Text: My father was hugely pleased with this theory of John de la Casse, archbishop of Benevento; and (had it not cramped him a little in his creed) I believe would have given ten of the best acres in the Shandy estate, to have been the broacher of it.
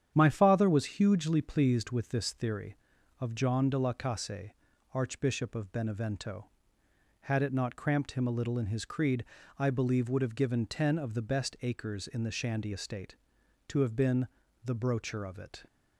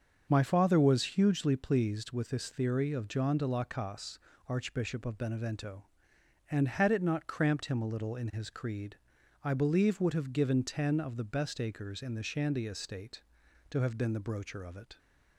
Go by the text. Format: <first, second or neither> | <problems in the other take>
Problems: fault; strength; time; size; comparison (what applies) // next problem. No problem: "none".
second | starts louder than the rest; strong; until 1.1 s; 9 dB; also in the second // skips "and"; at 6.8 s // pauses between "been" and "the"; slight; at 14.2 s; 0.36 s long